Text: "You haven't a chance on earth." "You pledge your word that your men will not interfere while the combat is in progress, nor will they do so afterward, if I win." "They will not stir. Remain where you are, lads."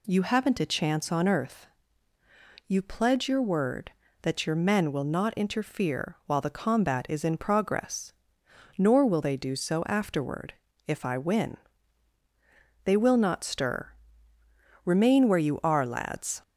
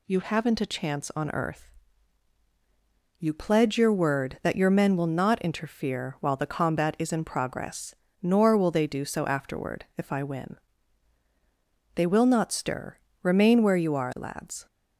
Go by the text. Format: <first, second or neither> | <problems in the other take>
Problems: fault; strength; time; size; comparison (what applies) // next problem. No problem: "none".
neither | none